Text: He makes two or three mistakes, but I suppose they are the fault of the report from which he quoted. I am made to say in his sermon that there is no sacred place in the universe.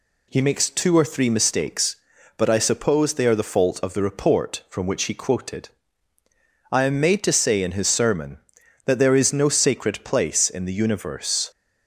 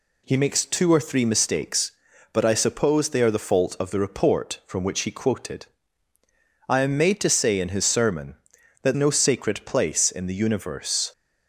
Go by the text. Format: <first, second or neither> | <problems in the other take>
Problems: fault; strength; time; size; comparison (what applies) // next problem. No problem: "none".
first | skips "there is"; at 8.9 s